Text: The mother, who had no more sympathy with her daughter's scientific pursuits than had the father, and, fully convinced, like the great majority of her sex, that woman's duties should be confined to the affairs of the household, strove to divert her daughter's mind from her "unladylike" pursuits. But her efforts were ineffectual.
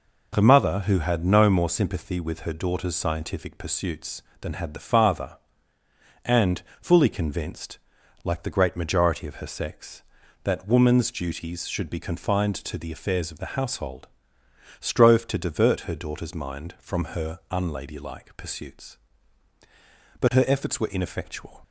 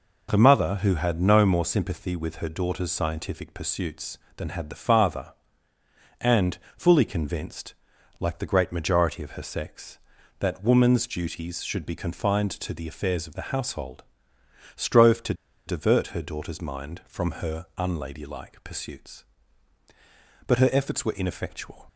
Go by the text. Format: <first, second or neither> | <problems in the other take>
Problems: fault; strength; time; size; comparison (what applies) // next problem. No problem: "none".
first | pauses between "to" and "divert"; slight; at 15.3 s; 0.33 s long